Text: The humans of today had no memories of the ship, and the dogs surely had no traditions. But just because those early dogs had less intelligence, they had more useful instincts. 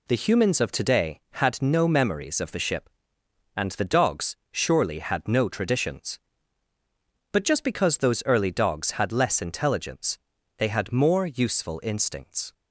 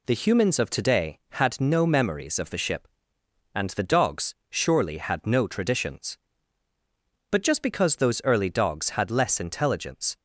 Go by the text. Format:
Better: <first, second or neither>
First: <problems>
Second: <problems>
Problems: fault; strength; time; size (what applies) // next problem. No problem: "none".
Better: first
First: pauses between "dogs" and "surely"; slight; at 4.3 s; 0.16 s long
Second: pauses between "dogs" and "surely"; slight; at 4.3 s; 0.16 s long // stops before "they had more useful instincts"; at 10.1 s